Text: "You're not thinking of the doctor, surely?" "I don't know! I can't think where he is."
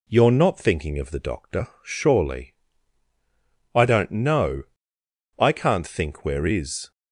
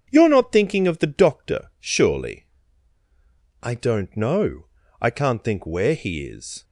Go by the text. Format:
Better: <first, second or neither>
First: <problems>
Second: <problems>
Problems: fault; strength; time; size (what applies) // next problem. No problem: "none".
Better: second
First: skips "he"; at 6.4 s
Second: none